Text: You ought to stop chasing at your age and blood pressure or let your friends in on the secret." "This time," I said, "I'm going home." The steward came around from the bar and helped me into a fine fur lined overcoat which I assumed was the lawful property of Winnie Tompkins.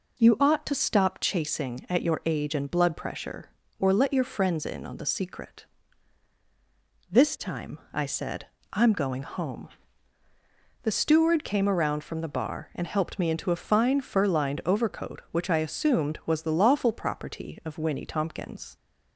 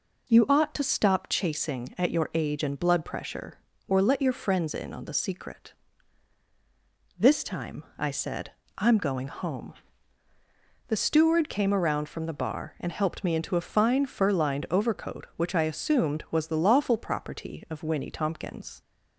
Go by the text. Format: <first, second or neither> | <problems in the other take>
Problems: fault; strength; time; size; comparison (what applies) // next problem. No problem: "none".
neither | none